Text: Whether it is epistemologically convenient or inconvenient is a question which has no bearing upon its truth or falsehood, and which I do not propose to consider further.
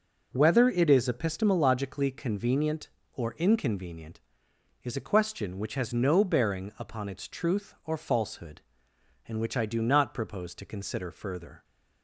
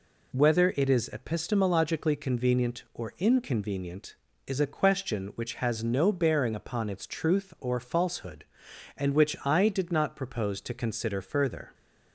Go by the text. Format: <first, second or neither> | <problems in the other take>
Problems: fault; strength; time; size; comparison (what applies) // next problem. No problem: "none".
first | says "did" for "do"; at 9.6 s